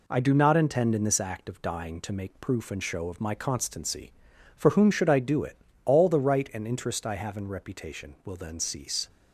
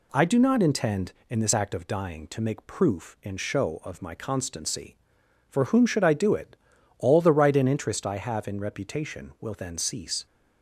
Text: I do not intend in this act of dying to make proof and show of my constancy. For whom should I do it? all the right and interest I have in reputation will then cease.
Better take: neither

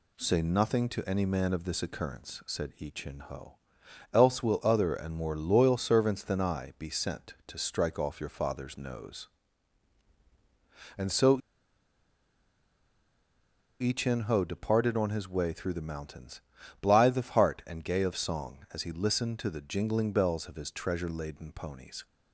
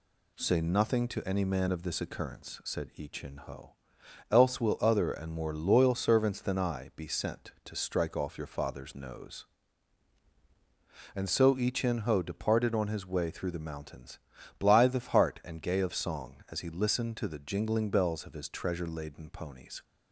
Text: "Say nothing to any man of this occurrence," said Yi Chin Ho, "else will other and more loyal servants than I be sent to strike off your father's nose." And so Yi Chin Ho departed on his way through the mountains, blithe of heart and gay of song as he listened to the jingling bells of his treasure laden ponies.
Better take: second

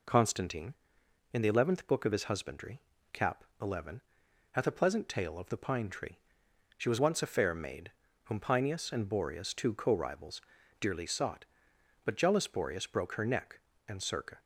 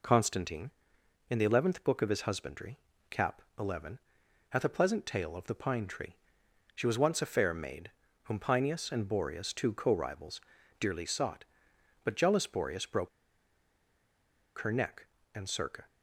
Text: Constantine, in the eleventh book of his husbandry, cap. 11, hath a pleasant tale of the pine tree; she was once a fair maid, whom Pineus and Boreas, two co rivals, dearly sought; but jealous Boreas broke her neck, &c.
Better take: first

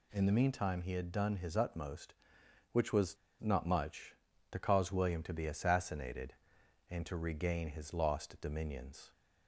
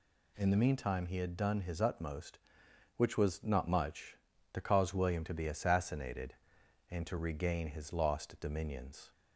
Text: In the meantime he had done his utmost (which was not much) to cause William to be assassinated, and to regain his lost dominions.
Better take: second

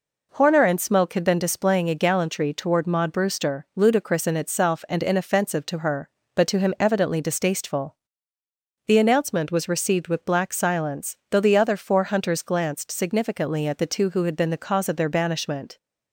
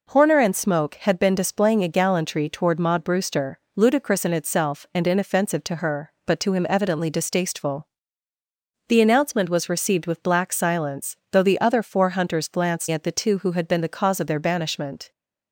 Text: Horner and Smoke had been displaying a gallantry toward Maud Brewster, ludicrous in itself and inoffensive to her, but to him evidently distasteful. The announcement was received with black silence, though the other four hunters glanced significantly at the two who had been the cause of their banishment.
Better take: first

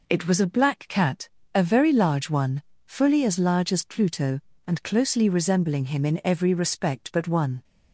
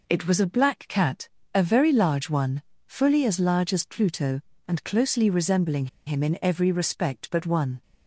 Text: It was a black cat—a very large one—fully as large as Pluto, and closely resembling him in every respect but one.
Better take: first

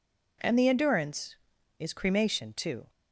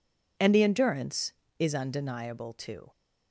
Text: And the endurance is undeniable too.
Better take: second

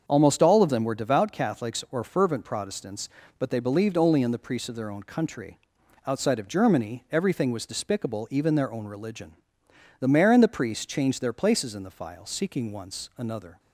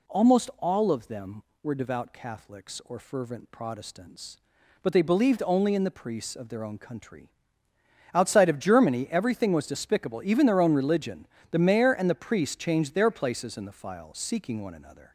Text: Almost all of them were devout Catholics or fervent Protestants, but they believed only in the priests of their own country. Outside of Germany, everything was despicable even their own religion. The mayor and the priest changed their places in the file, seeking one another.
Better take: second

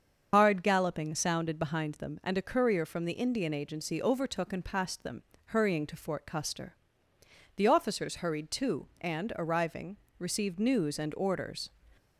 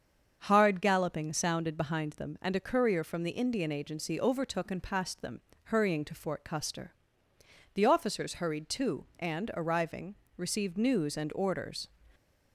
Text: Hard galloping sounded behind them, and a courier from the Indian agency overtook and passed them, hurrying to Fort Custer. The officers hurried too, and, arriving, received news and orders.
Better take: second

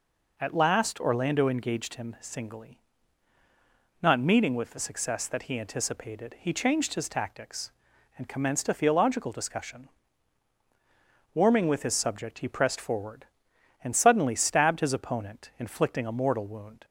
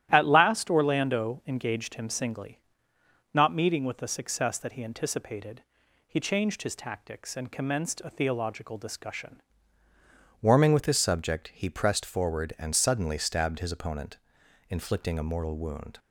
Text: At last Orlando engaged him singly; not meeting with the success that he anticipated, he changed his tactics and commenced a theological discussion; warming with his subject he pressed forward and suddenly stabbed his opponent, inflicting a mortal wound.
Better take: first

